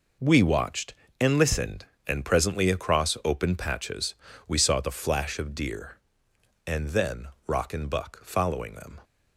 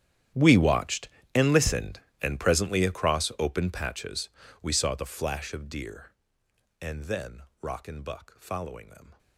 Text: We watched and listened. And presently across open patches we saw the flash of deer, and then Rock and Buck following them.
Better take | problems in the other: first | gets quieter; strong; throughout; 20.5 dB // pauses between "patches" and "we"; slight; at 4.2 s; 0.32 s long; slight in the first // pauses between "then" and "Rock"; slight; at 7.4 s; 0.18 s long; slight in the first

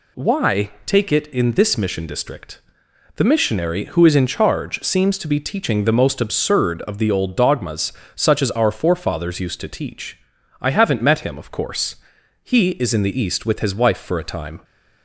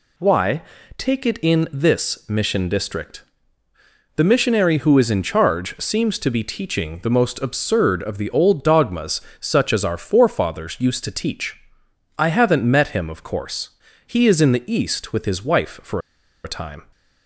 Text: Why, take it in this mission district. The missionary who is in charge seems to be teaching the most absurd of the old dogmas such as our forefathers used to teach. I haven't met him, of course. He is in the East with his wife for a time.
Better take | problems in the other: first | pauses between "dogmas" and "such"; slight; at 9.2 s; 0.20 s long; slight in the first // pauses between "for" and "a"; at 16.0 s; 0.44 s long

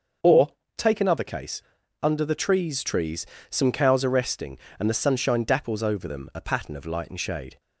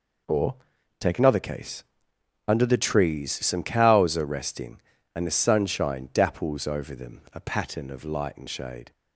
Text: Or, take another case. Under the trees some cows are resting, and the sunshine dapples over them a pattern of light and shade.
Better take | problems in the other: second | starts louder than the rest; until 1.5 s; 6.5 dB // says "trees" twice; at 2.8 s

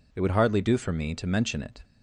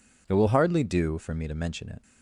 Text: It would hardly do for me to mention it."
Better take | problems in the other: first | says "will" for "would"; at 0.3 s

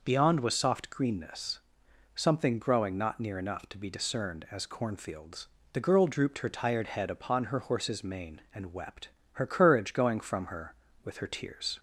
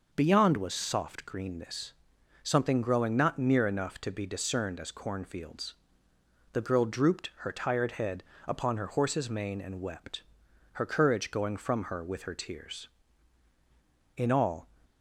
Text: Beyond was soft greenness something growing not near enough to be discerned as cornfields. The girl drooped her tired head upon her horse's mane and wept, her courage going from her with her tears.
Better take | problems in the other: first | pauses between "greenness" and "something"; noticeable; at 1.9 s; 0.50 s long; noticeable in the first // pauses between "head" and "upon"; slight; at 8.2 s; 0.24 s long // goes on to say "In all"; from 14.1 s on; 0.52 s long

